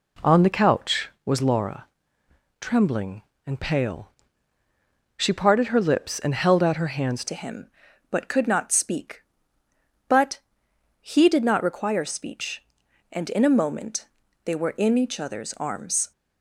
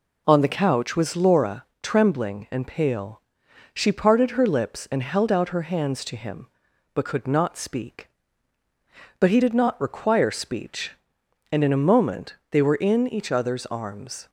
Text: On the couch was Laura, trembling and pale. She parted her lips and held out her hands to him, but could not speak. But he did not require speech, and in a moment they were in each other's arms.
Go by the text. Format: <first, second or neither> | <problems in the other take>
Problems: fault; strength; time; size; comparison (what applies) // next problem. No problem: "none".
second | changes voice at "to"; from 7.2 s on; 8.9 s long // pauses between "But" and "he"; noticeable; at 10.3 s; 0.60 s long // pauses between "moment" and "they"; at 14.0 s; 0.38 s long; slight in the second